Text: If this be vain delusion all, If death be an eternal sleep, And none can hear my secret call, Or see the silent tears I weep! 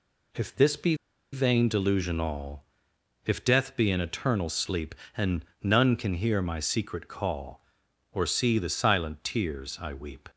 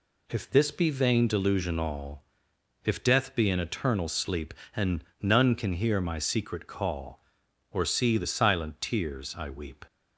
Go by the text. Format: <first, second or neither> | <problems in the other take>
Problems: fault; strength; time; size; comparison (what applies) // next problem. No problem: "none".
second | pauses between "be" and "vain"; at 0.9 s; 0.37 s long // pauses between "And" and "none"; slight; at 5.4 s; 0.18 s long; slight in the second